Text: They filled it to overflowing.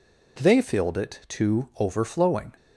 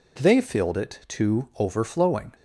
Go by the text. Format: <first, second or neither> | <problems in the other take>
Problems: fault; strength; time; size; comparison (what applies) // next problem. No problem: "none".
neither | none